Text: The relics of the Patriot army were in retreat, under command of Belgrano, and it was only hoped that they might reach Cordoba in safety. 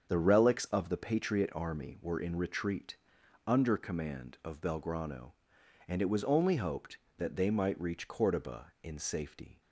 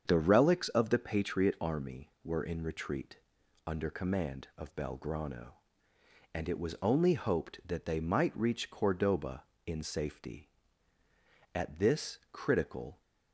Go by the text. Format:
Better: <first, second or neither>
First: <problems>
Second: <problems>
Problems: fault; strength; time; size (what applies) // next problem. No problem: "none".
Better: first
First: starts louder than the rest; strong; until 1.0 s; 7 dB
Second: starts louder than the rest; strong; until 1.0 s; 7 dB // goes on to say "At this critical"; from 11.5 s on; 1.4 s long